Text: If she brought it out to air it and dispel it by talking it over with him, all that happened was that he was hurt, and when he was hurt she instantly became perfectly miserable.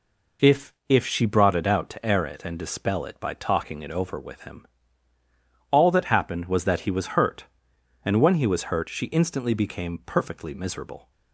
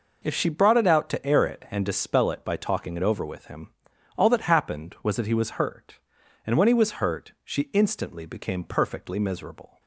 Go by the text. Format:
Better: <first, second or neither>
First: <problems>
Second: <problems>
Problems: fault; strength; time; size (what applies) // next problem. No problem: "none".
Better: second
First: says "If" twice; at 0.8 s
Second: none